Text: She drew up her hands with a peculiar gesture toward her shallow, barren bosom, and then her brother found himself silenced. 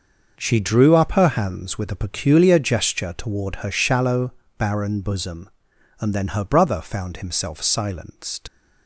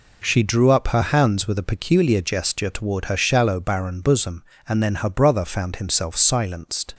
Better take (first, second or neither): second